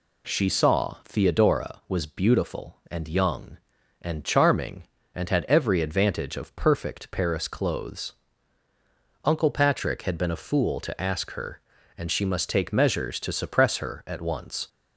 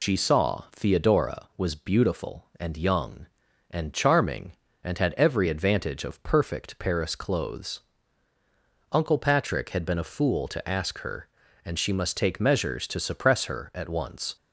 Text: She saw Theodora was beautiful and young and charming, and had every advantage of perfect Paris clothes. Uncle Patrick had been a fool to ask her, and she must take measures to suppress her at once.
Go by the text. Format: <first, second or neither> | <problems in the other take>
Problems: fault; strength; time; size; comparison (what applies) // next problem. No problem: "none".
first | loses the start of "She"; at 0.0 s; 95 ms